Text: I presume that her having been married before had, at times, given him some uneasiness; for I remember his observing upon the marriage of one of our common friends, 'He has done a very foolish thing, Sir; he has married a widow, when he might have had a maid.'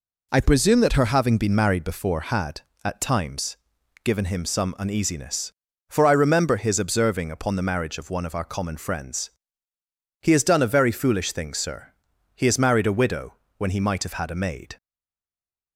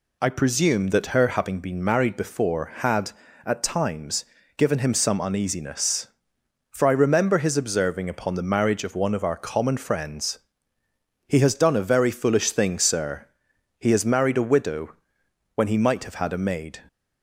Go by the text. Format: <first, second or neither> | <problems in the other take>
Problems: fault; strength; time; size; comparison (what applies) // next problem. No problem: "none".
second | stays silent after the last word; from 14.7 s on; 1.0 s long